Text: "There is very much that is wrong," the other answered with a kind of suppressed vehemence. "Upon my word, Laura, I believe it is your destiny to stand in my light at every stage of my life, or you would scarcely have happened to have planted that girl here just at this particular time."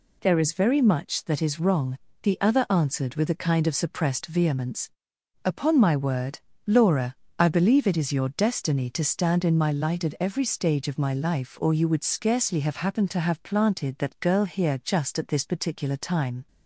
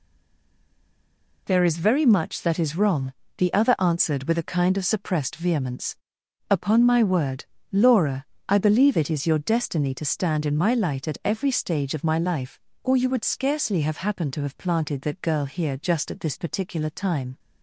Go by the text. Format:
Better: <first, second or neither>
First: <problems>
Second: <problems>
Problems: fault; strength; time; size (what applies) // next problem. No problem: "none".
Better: first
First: none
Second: stays silent before the first word; noticeable; until 1.4 s; 1.4 s long